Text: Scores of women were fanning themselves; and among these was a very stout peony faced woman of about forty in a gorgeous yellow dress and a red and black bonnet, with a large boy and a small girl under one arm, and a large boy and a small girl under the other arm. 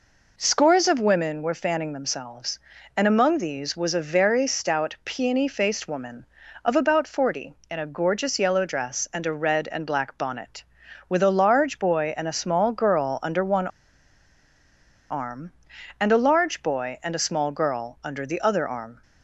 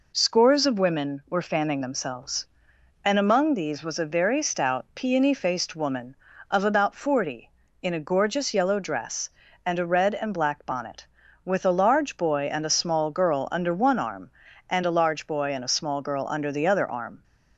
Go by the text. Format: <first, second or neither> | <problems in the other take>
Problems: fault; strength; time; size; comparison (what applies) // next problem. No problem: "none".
second | pauses between "one" and "arm"; strong; at 13.6 s; 1.4 s long